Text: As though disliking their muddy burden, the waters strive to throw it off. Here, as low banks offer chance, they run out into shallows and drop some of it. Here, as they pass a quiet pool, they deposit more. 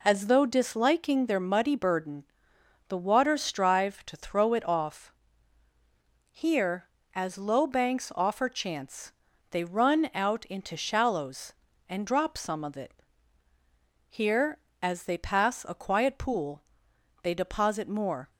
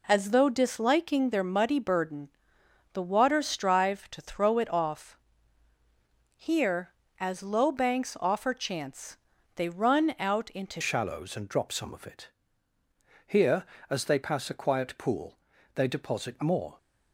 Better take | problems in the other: first | changes voice at "shallows"; from 10.8 s on; 5.9 s long

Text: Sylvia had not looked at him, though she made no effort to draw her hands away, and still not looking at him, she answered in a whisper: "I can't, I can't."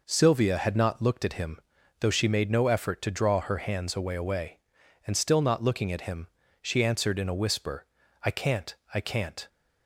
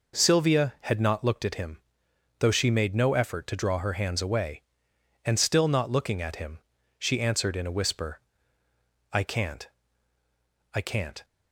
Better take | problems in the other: second | says "away" twice; at 4.1 s

